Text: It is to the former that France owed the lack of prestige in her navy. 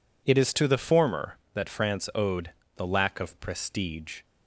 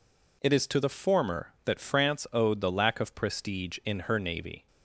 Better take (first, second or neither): second